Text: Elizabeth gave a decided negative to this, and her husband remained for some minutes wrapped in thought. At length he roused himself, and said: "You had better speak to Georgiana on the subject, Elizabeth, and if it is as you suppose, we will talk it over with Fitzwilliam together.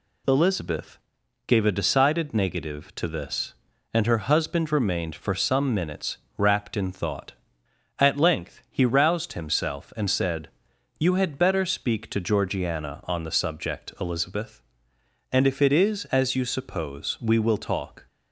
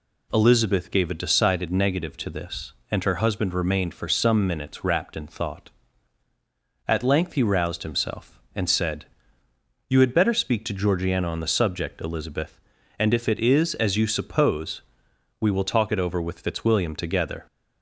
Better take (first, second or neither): second